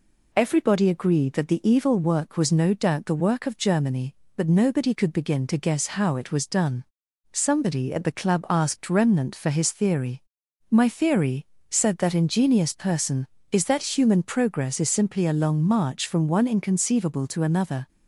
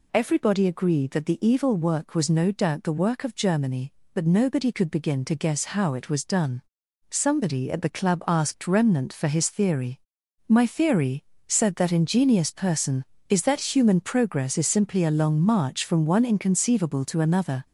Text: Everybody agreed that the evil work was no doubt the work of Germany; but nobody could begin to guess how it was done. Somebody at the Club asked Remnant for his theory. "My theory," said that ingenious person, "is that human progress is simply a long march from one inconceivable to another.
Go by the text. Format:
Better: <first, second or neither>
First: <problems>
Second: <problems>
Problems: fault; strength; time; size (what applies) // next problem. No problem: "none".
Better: first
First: none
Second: gets louder; noticeable; throughout; 4 dB